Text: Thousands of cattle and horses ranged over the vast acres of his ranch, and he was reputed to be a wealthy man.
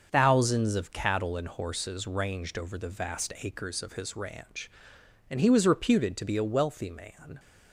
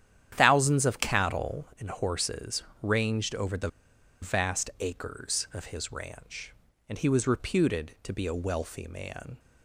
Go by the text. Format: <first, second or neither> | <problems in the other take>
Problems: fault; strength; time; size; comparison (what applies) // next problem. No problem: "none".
first | starts louder than the rest; strong; until 1.4 s; 10 dB; also in the first // pauses between "horses" and "ranged"; slight; at 2.6 s; 0.18 s long // pauses between "the" and "vast"; noticeable; at 3.6 s; 0.52 s long